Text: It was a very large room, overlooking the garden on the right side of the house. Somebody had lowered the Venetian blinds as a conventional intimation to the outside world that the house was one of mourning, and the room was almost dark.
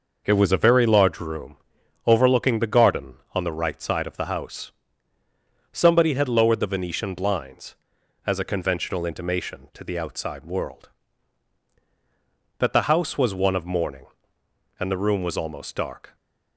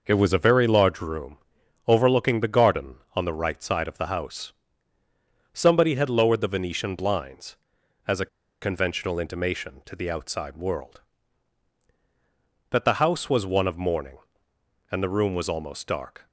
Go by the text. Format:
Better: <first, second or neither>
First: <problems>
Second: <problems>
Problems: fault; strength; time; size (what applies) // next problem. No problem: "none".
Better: first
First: none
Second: pauses between "a" and "conventional"; slight; at 8.2 s; 0.35 s long